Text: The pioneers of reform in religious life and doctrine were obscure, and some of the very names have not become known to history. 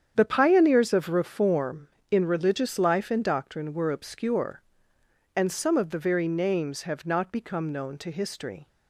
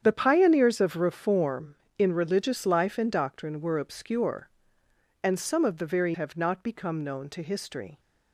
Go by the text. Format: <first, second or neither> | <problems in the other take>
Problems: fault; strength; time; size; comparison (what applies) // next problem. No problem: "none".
first | starts louder than the rest; strong; until 1.0 s; 8.5 dB; strong in the first // skips "names"; at 6.1 s